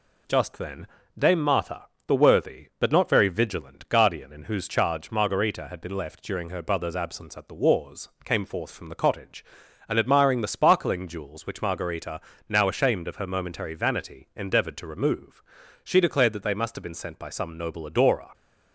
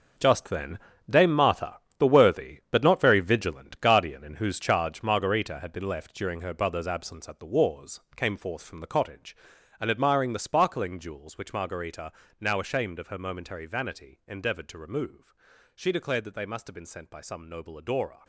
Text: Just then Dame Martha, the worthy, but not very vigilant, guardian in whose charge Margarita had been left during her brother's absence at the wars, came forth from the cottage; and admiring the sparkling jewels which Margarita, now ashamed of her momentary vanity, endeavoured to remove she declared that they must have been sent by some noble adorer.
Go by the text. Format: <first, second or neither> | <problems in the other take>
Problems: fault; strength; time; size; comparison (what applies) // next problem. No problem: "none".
first | gets quieter; strong; throughout; 12 dB // pauses between "then" and "Dame"; slight; at 0.7 s; 0.30 s long; slight in the first // pauses between "remove" and "she"; at 15.3 s; 0.44 s long; also in the first